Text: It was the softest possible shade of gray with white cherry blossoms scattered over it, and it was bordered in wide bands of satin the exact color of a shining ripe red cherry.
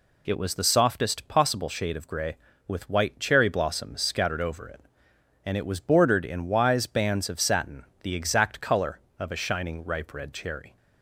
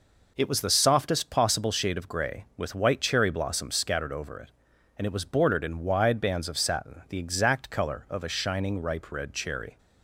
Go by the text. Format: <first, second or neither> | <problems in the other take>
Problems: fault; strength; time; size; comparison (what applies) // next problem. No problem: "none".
second | says "wise" for "wide"; at 6.4 s // pauses between "satin" and "the"; slight; at 7.8 s; 0.18 s long